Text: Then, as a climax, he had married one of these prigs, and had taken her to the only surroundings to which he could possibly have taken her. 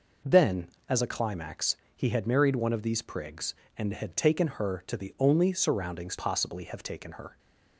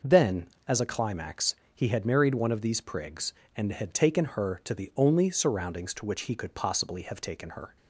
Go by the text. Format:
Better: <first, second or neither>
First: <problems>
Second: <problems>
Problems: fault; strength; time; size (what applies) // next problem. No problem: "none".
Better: second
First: skips "to which he could"; at 6.1 s // stays silent after the last word; slight; from 7.2 s on; 0.5 s long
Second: none